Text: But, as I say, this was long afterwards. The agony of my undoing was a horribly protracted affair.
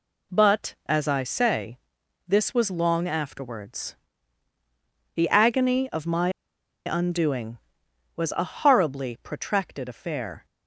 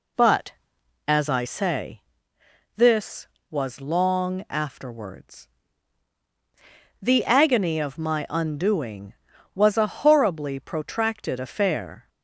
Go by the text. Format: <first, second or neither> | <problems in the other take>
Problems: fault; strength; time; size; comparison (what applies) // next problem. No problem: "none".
second | pauses between "my" and "undoing"; noticeable; at 6.2 s; 0.56 s long